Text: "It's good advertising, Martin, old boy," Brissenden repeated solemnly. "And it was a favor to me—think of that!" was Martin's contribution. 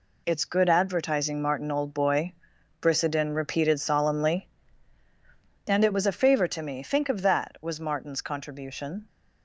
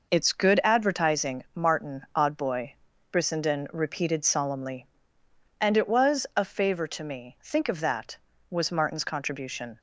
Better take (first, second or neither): first